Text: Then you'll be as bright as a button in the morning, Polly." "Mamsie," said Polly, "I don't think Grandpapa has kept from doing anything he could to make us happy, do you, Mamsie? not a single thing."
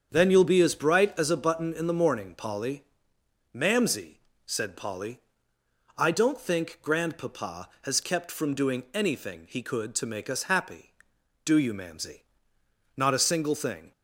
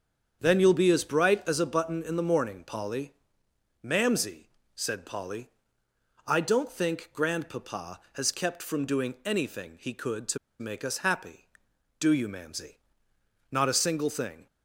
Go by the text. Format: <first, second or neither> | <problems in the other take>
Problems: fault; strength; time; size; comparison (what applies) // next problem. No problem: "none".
first | starts louder than the rest; strong; until 1.4 s; 7.5 dB; strong in the first // pauses between "to" and "make"; slight; at 10.3 s; 0.22 s long